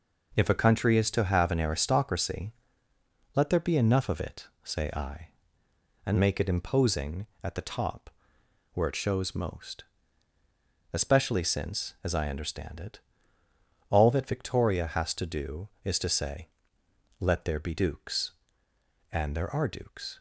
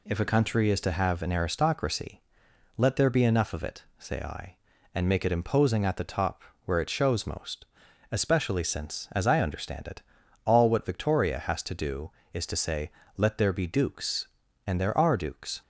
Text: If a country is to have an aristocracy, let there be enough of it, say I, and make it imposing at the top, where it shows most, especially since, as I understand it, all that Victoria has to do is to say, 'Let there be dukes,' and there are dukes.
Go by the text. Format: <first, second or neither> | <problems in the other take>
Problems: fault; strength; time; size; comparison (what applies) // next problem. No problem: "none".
first | says "what" for "that"; at 10.6 s